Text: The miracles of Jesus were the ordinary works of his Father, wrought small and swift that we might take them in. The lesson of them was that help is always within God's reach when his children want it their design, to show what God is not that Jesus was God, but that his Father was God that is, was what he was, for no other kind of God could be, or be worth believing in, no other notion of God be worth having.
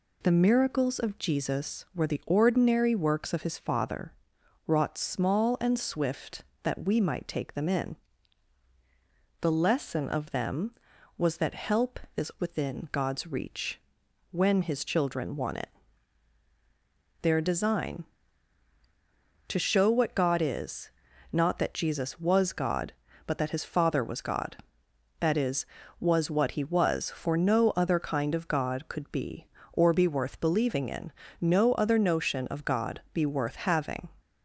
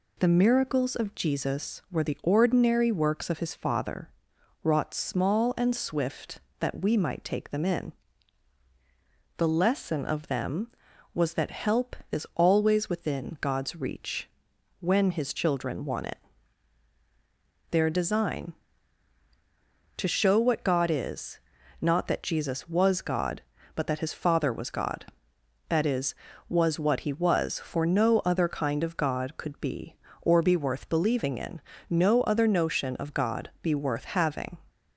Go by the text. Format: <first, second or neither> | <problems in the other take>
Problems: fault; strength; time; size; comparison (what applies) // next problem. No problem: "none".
second | skips "always"; at 12.3 s // pauses between "reach" and "when"; noticeable; at 13.7 s; 0.54 s long; noticeable in the second // pauses between "it" and "their"; strong; at 15.6 s; 1.5 s long; strong in the second // pauses between "is" and "not"; at 20.8 s; 0.42 s long; also in the second